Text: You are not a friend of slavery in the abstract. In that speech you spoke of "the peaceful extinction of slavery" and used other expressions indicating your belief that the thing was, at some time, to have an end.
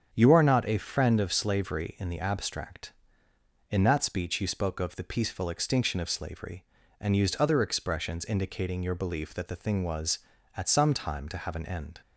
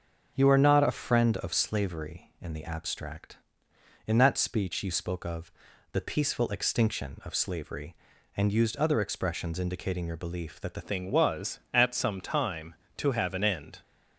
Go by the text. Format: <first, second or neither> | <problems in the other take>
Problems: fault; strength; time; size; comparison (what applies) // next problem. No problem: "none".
first | starts louder than the rest; until 1.3 s; 6.5 dB; strong in the first // pauses between "of" and "the"; at 5.5 s; 0.40 s long // changes voice at "thing"; from 10.8 s on; 3.0 s long